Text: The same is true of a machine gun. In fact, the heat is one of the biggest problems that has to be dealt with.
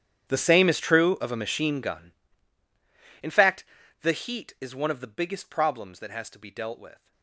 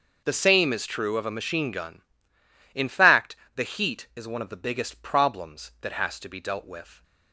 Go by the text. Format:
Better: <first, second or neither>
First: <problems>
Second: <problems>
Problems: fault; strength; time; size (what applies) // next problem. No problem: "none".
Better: second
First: gets quieter; strong; throughout; 21.5 dB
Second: none